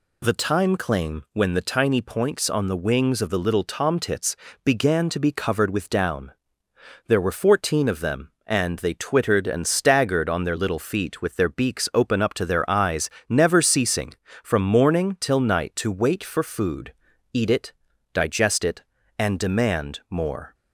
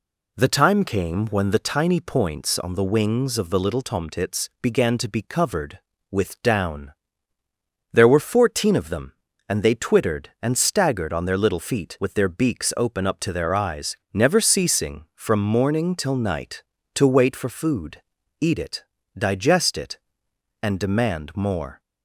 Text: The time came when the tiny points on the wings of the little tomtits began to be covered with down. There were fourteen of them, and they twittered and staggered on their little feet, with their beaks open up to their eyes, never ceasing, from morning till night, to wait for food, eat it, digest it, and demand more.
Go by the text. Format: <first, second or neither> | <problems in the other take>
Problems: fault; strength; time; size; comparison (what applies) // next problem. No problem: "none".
second | says "claim" for "came"; at 0.7 s // pauses between "tomtits" and "began"; slight; at 4.3 s; 0.26 s long